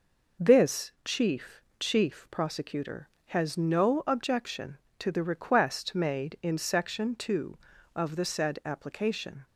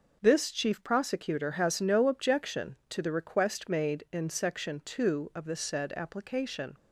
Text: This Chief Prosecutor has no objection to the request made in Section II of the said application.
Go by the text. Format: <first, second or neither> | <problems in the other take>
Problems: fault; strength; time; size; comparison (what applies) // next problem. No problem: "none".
second | says "Chief" twice; at 1.7 s